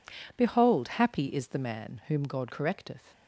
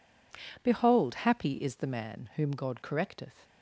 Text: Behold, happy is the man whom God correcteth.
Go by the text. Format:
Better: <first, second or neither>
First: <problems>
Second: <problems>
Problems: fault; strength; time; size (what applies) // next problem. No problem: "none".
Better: neither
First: none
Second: none